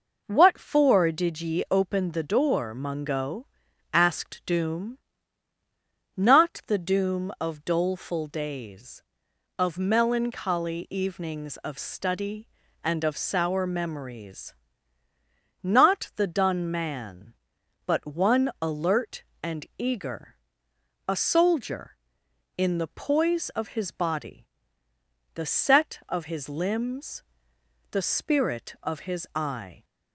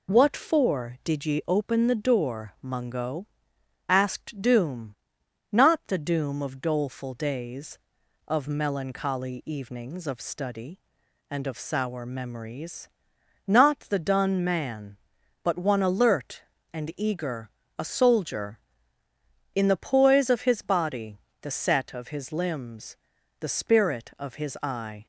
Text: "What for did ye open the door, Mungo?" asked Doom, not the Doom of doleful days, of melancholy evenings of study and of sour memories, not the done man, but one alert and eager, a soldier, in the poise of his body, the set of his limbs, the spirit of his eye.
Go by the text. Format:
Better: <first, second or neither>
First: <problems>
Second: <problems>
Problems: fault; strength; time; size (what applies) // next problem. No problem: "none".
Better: neither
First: none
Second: none